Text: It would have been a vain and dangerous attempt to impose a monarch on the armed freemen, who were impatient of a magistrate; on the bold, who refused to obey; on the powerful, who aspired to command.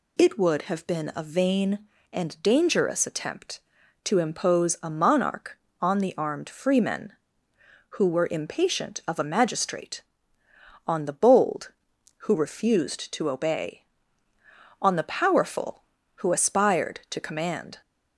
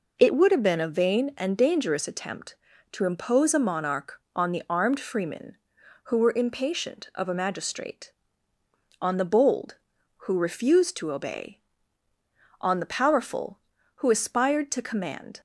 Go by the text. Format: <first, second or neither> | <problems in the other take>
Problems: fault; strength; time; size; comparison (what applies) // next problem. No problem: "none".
neither | none